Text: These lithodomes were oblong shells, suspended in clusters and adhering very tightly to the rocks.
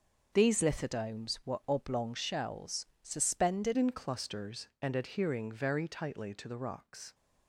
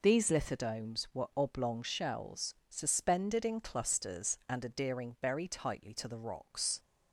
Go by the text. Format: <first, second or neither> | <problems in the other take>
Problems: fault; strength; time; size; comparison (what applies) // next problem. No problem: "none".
second | changes voice at "in"; from 3.7 s on; 3.4 s long